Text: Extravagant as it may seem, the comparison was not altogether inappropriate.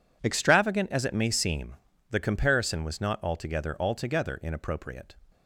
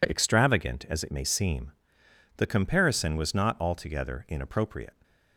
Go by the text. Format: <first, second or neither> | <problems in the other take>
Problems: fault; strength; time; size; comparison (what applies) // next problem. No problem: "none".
second | says "altogether" twice; at 3.8 s